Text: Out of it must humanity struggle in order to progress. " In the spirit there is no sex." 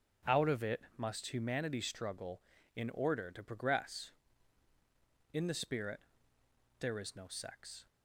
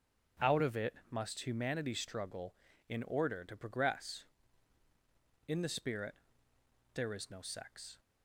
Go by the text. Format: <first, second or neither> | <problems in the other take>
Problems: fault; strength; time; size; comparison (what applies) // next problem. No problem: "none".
neither | starts louder than the rest; strong; the same in both // pauses between "it" and "must"; slight; the same in both // pauses between "spirit" and "there"; noticeable; the same in both